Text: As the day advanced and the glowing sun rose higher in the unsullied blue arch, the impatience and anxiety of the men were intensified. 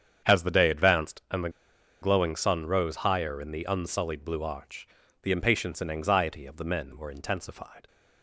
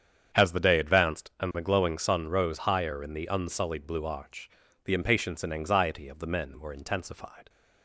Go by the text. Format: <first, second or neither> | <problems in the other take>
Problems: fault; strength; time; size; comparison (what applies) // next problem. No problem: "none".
second | starts louder than the rest; strong; until 1.3 s; 8 dB; strong in the second // pauses between "the" and "glowing"; noticeable; at 1.4 s; 0.52 s long